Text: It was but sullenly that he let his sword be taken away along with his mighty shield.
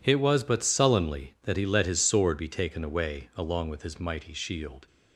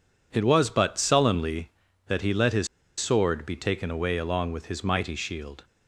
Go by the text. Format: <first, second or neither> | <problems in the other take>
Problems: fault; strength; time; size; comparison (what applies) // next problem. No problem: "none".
first | pauses between "his" and "sword"; slight; at 2.6 s; 0.32 s long